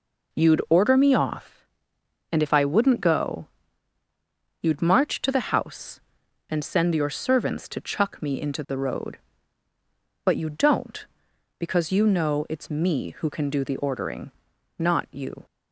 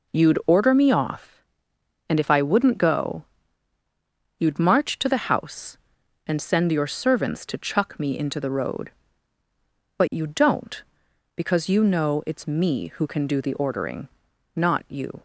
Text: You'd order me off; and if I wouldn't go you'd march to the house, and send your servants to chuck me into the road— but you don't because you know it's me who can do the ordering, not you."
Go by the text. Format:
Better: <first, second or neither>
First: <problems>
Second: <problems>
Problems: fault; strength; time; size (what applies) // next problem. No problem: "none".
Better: neither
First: pauses between "go" and "you'd"; at 3.4 s; 1.1 s long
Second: pauses between "go" and "you'd"; at 3.2 s; 1.1 s long